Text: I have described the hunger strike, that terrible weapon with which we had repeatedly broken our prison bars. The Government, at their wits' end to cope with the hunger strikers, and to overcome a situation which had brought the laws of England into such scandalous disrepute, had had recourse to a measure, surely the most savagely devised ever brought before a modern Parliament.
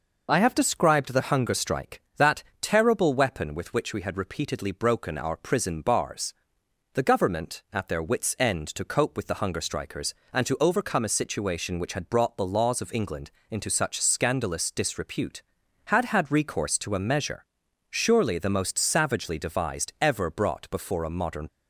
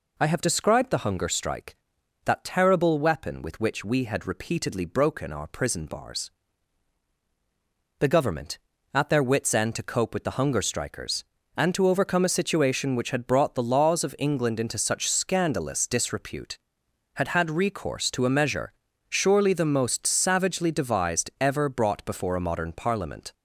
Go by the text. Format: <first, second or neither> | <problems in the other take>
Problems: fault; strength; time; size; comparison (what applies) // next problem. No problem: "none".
second | pauses between "that" and "terrible"; slight; at 2.4 s; 0.18 s long // pauses between "England" and "into"; slight; at 13.3 s; 0.18 s long // stops before "Parliament"; at 21.4 s